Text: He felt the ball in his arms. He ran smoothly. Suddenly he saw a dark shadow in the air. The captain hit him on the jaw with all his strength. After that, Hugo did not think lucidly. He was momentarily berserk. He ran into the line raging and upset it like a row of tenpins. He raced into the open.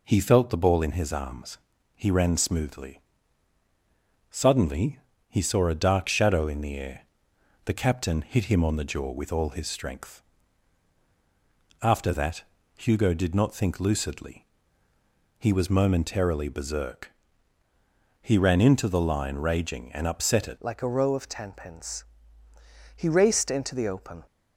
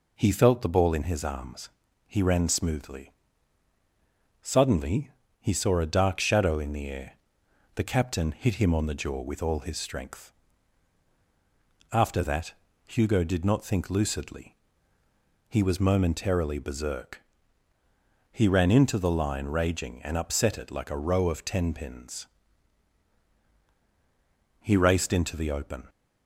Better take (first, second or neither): second